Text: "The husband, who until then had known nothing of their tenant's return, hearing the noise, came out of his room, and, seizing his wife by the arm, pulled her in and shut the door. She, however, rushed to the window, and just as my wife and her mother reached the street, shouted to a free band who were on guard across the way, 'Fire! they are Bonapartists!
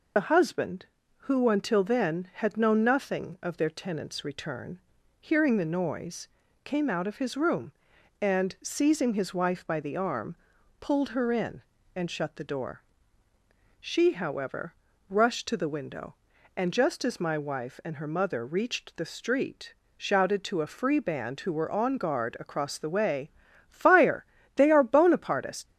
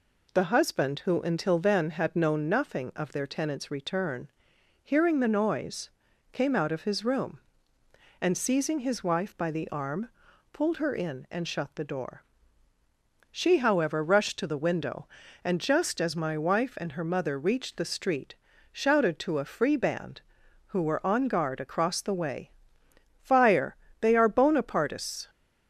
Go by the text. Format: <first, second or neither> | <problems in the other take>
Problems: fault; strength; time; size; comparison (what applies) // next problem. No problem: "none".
second | loses the start of "The"; at 0.1 s; 60 ms